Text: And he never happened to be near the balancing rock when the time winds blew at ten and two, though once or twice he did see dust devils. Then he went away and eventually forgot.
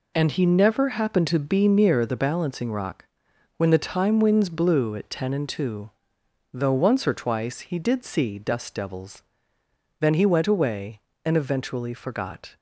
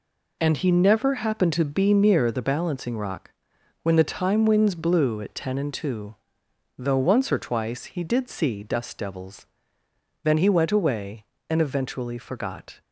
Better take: neither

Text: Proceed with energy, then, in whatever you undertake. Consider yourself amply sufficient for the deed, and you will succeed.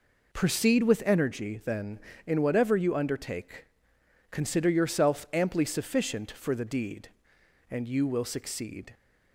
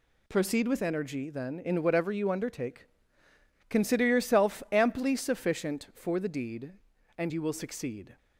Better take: neither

